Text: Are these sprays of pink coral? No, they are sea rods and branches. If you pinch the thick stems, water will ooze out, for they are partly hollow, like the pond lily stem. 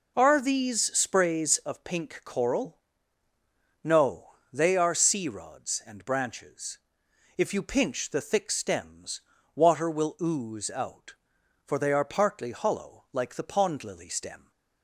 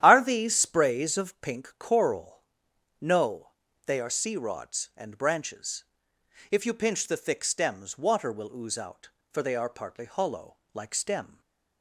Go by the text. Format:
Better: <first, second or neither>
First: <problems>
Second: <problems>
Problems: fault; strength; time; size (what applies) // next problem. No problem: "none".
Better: first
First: none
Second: starts louder than the rest; strong; until 1.0 s; 11 dB // skips "the pond lily"; at 10.9 s // stays silent after the last word; slight; from 11.3 s on; 0.5 s long